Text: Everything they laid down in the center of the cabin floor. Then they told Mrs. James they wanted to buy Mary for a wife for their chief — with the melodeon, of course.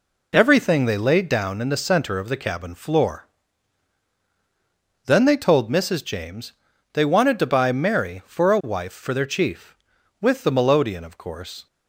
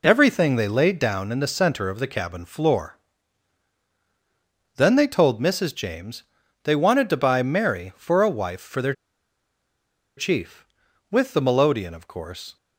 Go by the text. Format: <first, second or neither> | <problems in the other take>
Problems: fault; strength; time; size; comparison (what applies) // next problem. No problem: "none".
first | pauses between "James" and "they"; at 6.2 s; 0.40 s long; also in the first // pauses between "their" and "chief"; strong; at 8.9 s; 1.2 s long